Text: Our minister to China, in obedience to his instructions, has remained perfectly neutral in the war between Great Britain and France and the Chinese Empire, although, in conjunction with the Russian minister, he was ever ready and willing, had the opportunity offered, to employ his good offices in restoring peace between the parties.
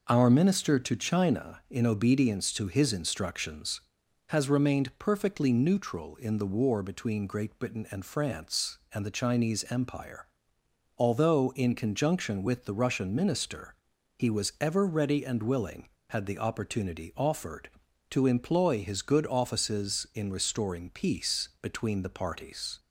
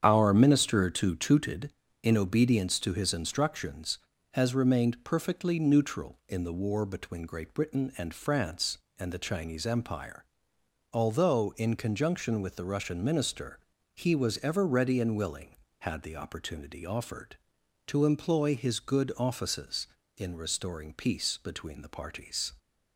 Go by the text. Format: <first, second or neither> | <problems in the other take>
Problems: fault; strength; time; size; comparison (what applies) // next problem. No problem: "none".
first | starts louder than the rest; strong; until 1.0 s; 8 dB // says "Tooted" for "China"; at 1.1 s